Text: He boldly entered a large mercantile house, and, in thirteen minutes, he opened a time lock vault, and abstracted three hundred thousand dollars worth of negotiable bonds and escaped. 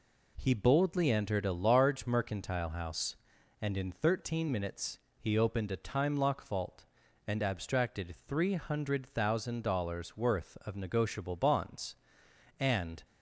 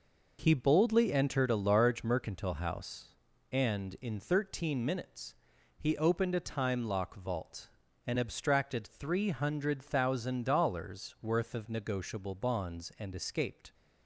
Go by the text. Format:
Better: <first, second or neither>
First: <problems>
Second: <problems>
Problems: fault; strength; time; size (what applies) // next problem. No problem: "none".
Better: second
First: stops before "escaped"; at 13.0 s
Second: none